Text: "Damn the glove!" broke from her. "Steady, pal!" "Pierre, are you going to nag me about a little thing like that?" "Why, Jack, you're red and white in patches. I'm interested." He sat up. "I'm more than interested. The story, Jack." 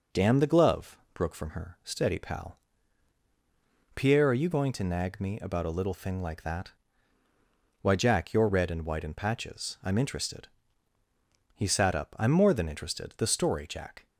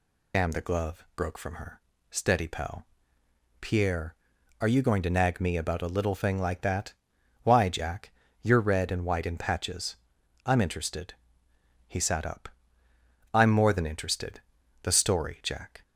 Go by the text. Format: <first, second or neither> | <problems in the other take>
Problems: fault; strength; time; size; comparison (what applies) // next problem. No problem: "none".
first | loses the start of "Damn"; at 0.3 s; 55 ms